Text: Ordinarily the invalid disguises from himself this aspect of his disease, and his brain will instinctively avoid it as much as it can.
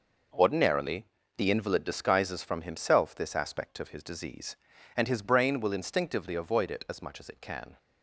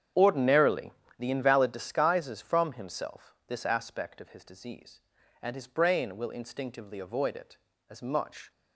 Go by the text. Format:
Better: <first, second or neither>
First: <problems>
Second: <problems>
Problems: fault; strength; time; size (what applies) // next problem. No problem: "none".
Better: first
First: pauses between "Ordinarily" and "the"; slight; at 1.0 s; 0.32 s long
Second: starts louder than the rest; strong; until 1.4 s; 8.5 dB // pauses between "Ordinarily" and "the"; slight; at 0.9 s; 0.30 s long // stops before "as it can"; at 8.5 s